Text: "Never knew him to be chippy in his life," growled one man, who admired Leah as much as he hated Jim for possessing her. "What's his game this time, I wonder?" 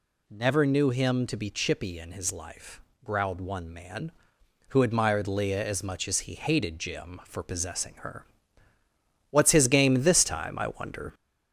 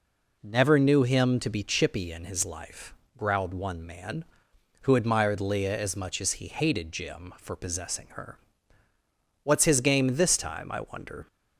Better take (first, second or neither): second